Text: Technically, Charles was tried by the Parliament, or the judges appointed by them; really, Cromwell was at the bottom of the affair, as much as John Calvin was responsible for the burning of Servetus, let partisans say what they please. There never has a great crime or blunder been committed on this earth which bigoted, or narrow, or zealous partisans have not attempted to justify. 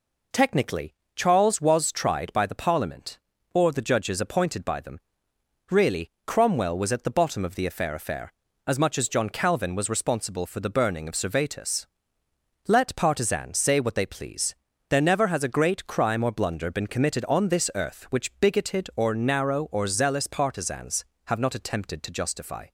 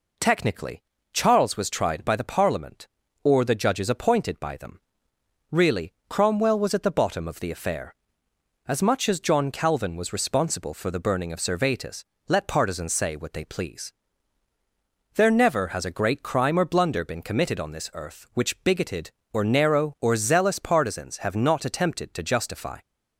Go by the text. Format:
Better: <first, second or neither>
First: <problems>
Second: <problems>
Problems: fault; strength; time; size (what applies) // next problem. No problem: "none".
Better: second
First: says "affair" twice; at 7.9 s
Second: none